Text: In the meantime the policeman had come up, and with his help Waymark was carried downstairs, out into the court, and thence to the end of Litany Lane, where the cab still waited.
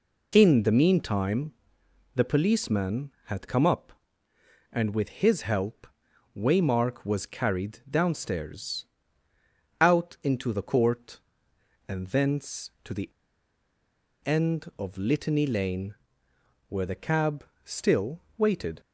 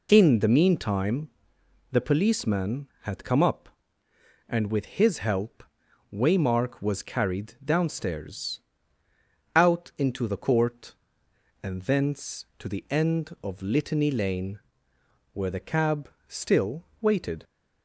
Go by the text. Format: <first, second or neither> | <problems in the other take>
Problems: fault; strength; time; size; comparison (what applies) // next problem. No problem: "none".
second | pauses between "meantime" and "the"; noticeable; at 1.5 s; 0.64 s long; noticeable in the second // pauses between "help" and "Waymark"; noticeable; at 5.8 s; 0.50 s long; noticeable in the second // pauses between "the" and "end"; at 13.1 s; 1.1 s long // pauses between "cab" and "still"; slight; at 17.4 s; 0.22 s long; slight in the second // pauses between "still" and "waited"; slight; at 18.2 s; 0.16 s long; slight in the second